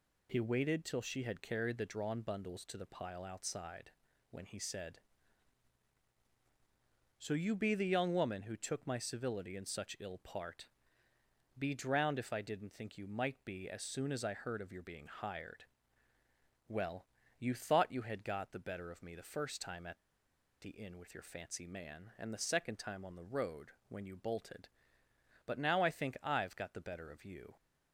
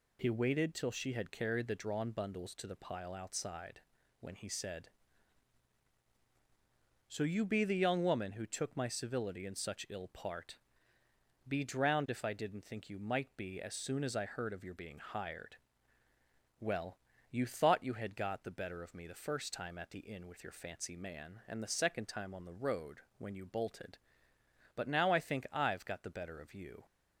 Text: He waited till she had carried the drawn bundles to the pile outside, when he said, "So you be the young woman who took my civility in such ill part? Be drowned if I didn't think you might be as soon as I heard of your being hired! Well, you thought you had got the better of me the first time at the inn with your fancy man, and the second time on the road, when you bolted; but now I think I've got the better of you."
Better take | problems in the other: second | pauses between "at" and "the"; noticeable; at 19.9 s; 0.63 s long

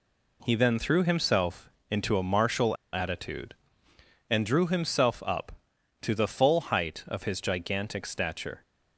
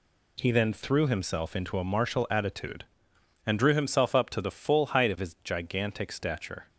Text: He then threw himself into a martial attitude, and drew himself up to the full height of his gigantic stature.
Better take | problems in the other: second | pauses between "himself" and "into"; slight; at 1.6 s; 0.20 s long // pauses between "martial" and "attitude"; slight; at 2.7 s; 0.18 s long

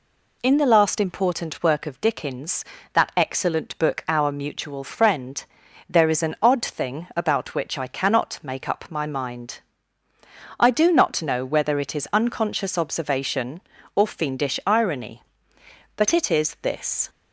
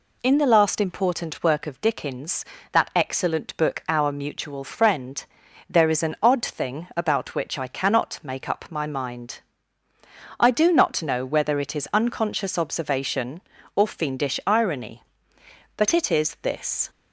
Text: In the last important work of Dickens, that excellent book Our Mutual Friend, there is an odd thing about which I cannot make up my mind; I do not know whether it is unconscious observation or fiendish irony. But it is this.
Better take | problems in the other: neither | none

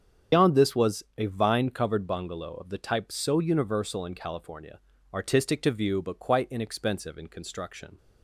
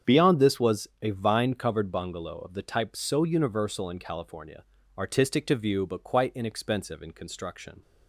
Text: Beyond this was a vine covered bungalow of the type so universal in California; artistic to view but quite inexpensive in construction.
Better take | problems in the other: second | loses the start of "Beyond"; at 0.3 s; 115 ms // starts louder than the rest; strong; until 1.4 s; 7.5 dB; strong in the second

